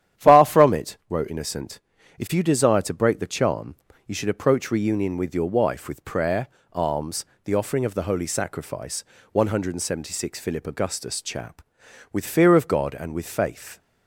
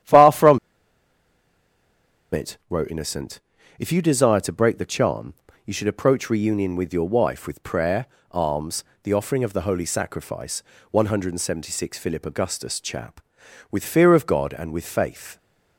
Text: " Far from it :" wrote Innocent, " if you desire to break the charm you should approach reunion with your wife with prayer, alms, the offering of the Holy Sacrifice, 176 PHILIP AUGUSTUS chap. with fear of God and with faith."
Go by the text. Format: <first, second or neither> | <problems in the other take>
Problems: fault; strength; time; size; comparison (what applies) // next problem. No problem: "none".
first | starts louder than the rest; strong; until 2.8 s; 10.5 dB; strong in the first // pauses between "from" and "it"; strong; at 0.5 s; 1.7 s long // pauses between "charm" and "you"; slight; at 5.3 s; 0.32 s long; slight in the first